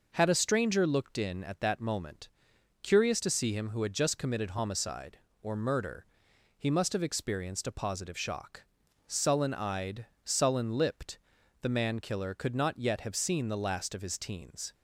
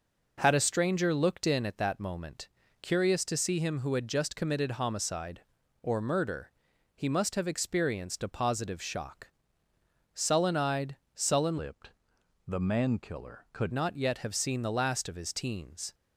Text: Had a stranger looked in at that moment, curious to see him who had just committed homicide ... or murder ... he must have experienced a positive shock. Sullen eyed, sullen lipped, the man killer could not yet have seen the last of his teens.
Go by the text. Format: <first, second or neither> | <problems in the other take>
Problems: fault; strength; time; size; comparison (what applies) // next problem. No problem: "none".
first | changes voice from "lipped" to "could"; from 11.5 to 13.7 s; 2.2 s long